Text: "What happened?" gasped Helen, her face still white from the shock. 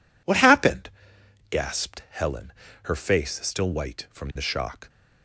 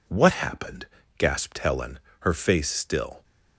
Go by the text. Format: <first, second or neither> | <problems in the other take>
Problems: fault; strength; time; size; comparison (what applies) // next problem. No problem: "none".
first | stops before "white from the shock"; at 3.2 s